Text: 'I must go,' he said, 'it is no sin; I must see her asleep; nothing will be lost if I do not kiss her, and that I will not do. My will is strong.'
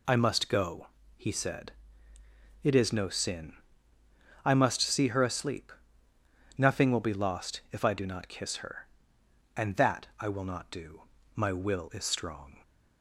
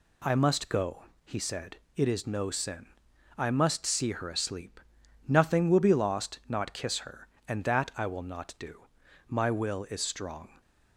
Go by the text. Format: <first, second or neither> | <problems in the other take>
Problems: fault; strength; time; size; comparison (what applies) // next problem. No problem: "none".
first | skips "if I do"; at 6.4 s